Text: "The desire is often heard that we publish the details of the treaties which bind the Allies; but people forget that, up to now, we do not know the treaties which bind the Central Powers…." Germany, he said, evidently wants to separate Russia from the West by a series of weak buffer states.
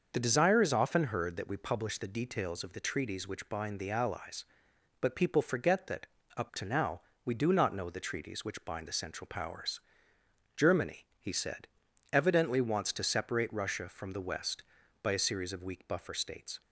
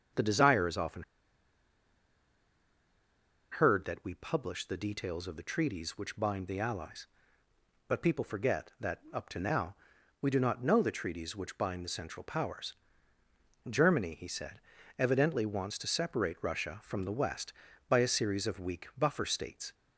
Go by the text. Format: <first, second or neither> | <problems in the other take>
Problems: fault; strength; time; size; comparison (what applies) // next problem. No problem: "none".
first | starts louder than the rest; until 3.6 s; 7 dB; noticeable in the first // pauses between "often" and "heard"; strong; at 1.0 s; 2.4 s long